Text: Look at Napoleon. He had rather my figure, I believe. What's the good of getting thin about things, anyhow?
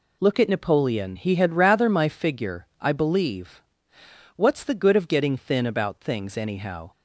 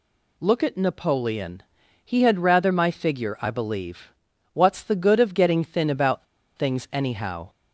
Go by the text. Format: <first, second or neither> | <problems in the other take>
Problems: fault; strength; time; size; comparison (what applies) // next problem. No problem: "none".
first | pauses between "about" and "things"; slight; at 6.2 s; 0.32 s long